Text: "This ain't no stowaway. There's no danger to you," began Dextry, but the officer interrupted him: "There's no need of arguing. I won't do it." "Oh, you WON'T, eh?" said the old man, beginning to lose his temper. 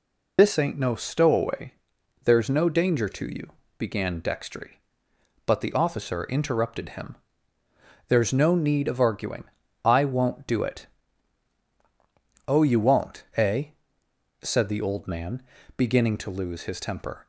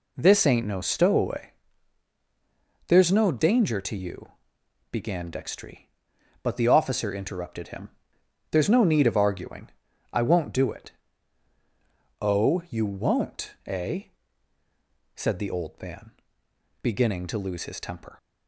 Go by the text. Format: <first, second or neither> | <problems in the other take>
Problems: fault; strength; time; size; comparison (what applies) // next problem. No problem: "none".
second | loses the start of "This"; at 0.3 s; 90 ms